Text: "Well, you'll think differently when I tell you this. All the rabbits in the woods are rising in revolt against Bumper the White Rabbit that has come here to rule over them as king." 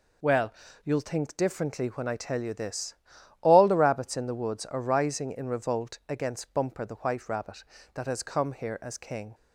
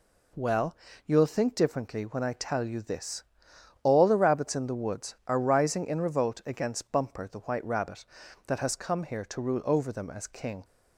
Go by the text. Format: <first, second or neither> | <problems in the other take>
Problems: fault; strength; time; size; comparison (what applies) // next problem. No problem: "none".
second | skips "to rule over them"; at 8.7 s